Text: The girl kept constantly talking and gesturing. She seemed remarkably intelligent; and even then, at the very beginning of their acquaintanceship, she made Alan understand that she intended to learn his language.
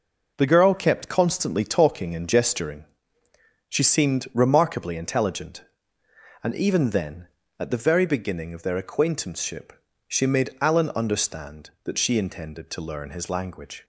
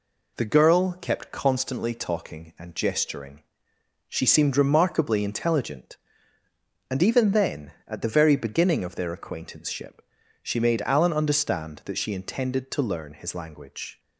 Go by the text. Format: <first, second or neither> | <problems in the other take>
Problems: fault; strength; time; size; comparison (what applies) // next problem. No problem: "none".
neither | none